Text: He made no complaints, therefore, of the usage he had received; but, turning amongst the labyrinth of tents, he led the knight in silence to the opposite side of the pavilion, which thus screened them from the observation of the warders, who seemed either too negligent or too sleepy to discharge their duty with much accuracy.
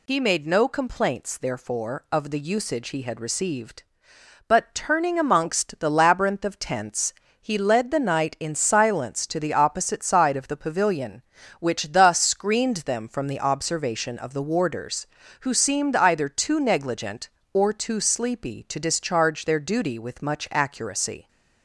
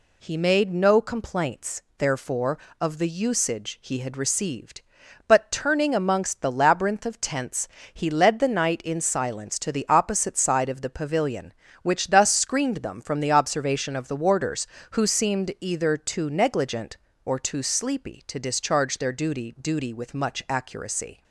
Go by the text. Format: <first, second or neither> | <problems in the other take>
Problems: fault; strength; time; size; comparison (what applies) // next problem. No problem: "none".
first | says "duty" twice; at 19.5 s